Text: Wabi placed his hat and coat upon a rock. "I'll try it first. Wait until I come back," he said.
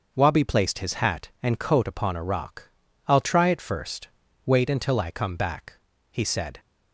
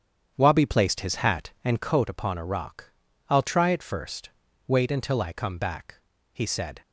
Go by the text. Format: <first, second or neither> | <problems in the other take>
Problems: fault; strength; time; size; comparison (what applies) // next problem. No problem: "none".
first | starts louder than the rest; strong; until 2.0 s; 8.5 dB